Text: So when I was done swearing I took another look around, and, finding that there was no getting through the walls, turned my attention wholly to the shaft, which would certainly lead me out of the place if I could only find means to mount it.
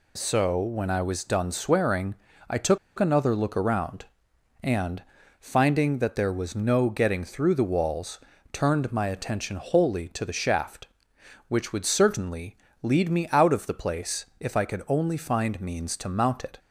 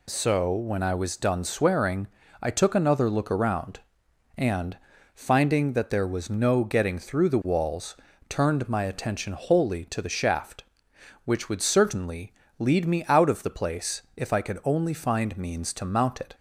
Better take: second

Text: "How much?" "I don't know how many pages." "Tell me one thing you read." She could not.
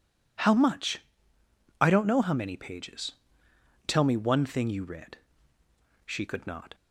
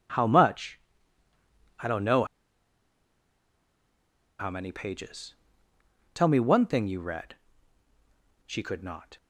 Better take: first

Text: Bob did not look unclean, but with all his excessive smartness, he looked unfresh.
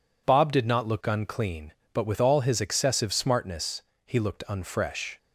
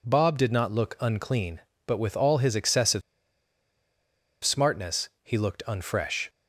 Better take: first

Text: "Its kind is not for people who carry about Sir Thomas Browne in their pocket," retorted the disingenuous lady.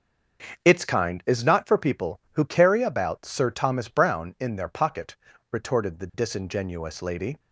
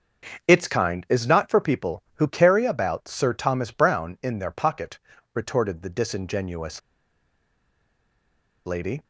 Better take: first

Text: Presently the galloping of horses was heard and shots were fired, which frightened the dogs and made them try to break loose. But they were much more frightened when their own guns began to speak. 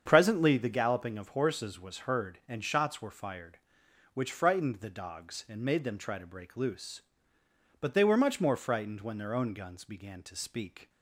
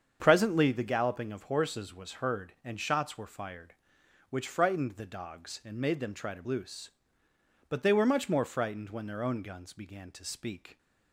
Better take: first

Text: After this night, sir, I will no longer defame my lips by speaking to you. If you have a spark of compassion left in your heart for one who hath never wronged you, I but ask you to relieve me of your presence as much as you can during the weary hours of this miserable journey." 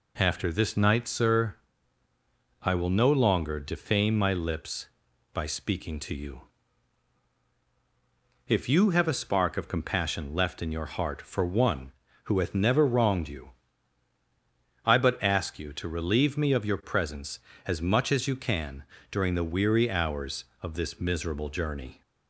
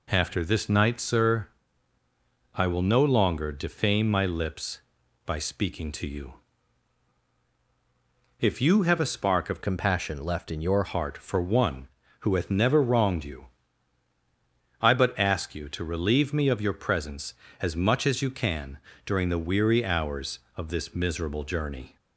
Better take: first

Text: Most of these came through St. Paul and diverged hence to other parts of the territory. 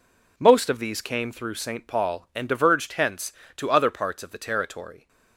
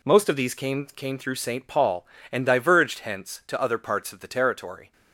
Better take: first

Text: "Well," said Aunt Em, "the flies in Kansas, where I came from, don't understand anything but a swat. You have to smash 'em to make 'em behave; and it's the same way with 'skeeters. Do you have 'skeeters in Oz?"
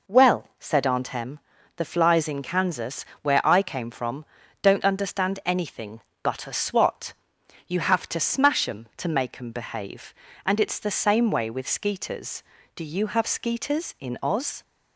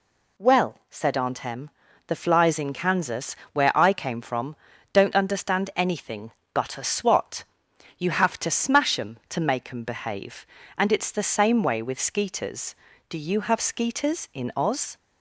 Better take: second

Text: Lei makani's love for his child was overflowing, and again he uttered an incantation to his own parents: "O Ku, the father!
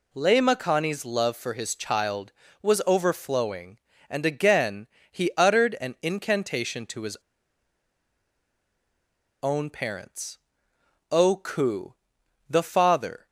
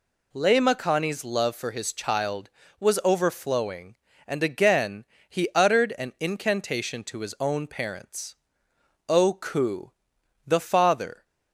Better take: second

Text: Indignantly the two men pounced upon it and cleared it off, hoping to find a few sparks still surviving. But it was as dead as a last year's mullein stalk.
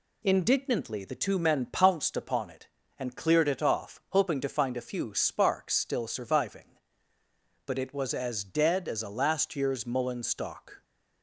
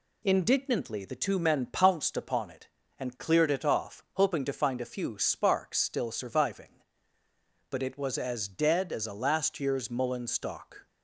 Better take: neither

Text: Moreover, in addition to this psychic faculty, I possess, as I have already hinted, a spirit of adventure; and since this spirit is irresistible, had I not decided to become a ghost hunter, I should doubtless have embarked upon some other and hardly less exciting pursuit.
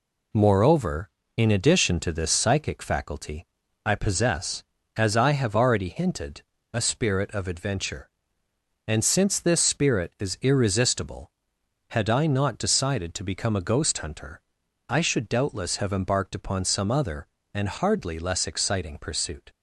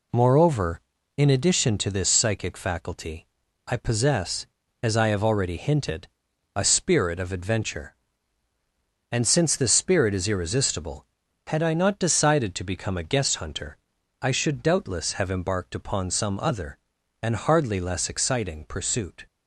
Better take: first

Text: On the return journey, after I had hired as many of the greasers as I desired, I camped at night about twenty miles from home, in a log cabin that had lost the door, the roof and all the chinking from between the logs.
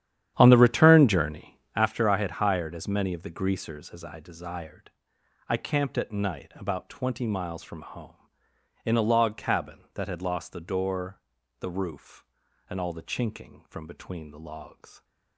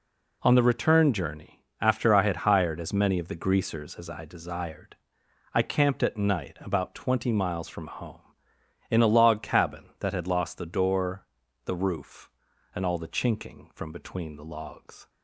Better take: second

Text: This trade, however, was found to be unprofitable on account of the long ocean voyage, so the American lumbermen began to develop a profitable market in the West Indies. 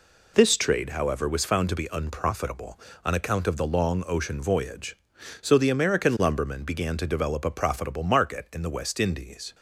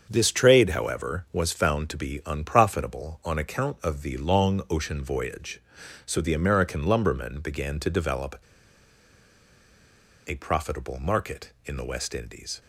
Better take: first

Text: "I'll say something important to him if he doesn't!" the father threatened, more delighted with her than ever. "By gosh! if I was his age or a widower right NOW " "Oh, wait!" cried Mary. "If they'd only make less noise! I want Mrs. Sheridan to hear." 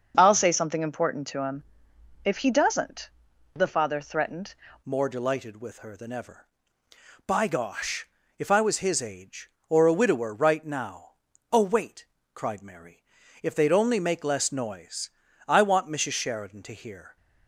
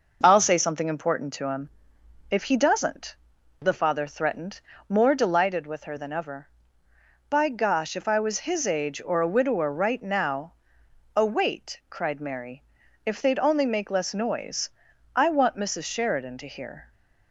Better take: second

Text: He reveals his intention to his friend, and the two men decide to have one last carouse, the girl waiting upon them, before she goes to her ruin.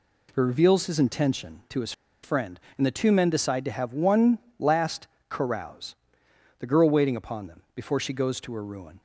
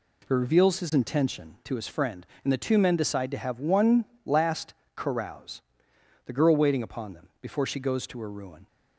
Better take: second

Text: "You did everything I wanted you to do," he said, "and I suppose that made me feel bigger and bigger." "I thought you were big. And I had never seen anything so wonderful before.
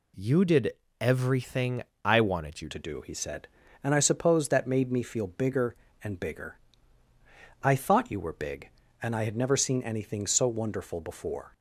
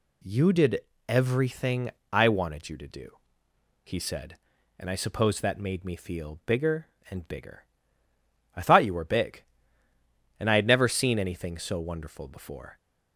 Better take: second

